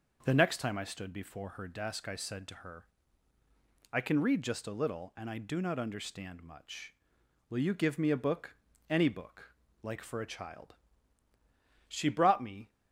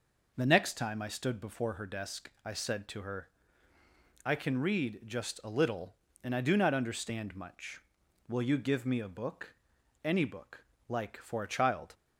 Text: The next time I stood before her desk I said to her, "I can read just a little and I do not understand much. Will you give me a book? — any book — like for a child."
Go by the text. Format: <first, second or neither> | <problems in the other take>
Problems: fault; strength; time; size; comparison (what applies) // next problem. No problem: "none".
second | goes on to say "She brought me"; noticeable; from 11.8 s on; 0.82 s long